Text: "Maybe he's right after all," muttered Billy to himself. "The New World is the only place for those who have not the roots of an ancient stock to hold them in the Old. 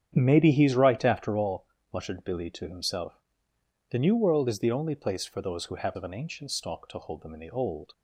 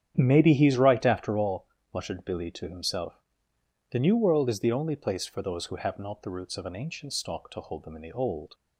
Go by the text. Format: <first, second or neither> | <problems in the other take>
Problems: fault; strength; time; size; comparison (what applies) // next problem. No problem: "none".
second | starts louder than the rest; strong; until 1.1 s; 9 dB; strong in the second // skips "not the roots"; at 5.9 s